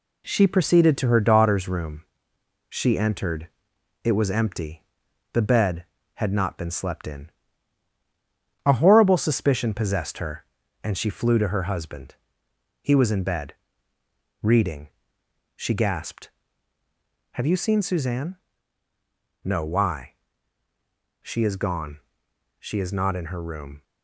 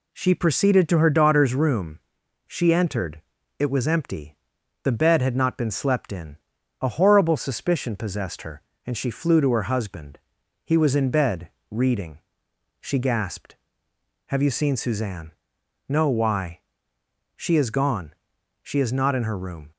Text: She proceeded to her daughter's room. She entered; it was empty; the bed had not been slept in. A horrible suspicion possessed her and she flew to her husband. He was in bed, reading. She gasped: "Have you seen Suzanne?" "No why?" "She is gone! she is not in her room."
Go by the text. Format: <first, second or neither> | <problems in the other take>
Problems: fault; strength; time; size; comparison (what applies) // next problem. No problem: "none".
second | gets quieter; noticeable; throughout; 5 dB